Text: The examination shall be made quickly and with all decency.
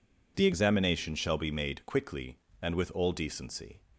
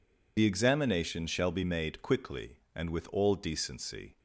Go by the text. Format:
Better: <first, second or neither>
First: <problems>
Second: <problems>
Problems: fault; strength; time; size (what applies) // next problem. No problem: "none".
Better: first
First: none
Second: loses the start of "The"; at 0.3 s; 55 ms